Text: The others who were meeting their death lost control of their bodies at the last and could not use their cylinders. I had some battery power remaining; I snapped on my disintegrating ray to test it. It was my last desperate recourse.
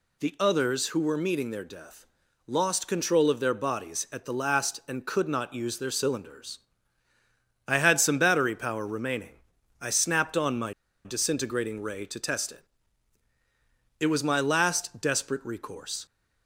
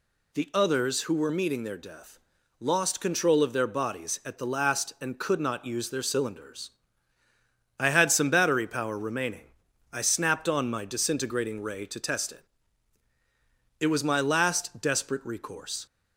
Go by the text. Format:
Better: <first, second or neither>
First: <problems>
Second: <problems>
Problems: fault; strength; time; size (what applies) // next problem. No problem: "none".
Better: second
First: pauses between "death" and "lost"; at 2.0 s; 0.40 s long // pauses between "my" and "disintegrating"; slight; at 10.7 s; 0.32 s long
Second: pauses between "death" and "lost"; at 2.1 s; 0.40 s long